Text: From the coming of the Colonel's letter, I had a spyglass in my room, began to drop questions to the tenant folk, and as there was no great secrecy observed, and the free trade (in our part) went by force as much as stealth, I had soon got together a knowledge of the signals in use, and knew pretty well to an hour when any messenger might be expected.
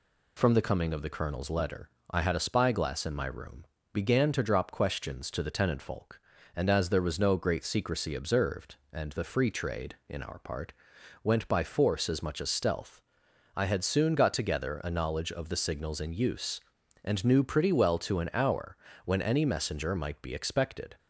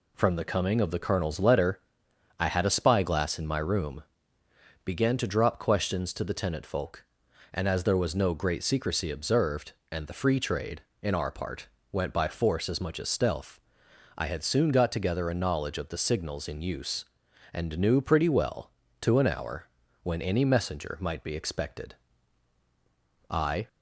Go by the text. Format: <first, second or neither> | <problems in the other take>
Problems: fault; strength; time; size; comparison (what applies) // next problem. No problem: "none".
first | pauses between "hour" and "when"; slight; at 19.6 s; 0.34 s long; slight in the first // goes on to say "I"; slight; from 23.2 s on; 0.38 s long